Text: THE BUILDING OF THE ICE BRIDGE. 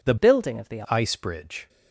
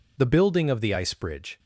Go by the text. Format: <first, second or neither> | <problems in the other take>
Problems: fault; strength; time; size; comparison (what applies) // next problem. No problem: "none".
second | changes voice from "BUILDING" to "THE"; from 0.1 to 0.8 s; 0.7 s long